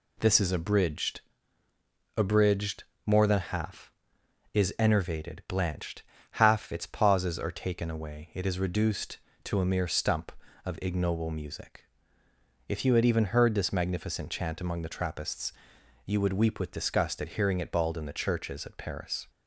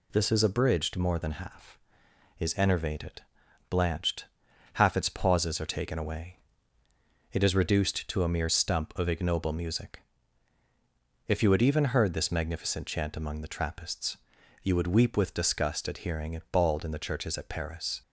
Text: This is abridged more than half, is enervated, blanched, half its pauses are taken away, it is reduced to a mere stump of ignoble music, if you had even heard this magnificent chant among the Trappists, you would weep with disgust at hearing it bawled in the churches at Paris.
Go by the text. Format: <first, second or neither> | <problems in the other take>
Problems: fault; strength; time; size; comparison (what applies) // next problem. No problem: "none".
second | says "abridged" twice; at 2.1 s